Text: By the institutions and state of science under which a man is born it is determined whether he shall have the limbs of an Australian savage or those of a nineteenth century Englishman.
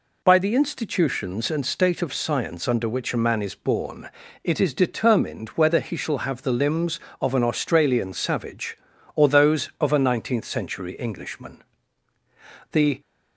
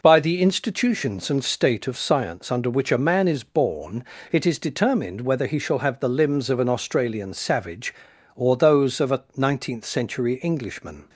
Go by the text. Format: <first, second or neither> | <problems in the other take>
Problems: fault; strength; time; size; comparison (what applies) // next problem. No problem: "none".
second | pauses between "born" and "it"; slight; at 4.1 s; 0.34 s long; slight in the second // goes on to say "The"; slight; from 12.7 s on; 0.28 s long